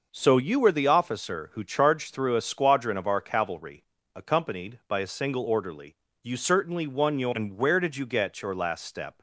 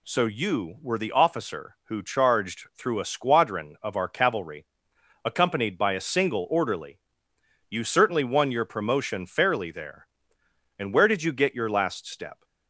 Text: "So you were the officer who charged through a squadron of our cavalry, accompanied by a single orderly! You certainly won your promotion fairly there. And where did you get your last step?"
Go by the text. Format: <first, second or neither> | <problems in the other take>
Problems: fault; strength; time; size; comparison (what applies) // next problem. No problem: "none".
second | skips "promotion fairly there"; at 7.3 s